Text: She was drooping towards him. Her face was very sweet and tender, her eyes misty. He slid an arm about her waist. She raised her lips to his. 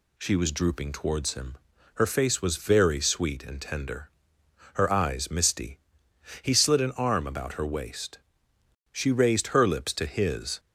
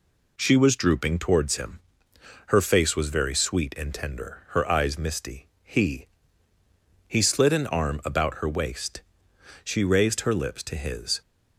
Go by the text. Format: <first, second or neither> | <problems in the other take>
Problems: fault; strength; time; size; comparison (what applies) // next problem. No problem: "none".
first | says "He" twice; at 7.0 s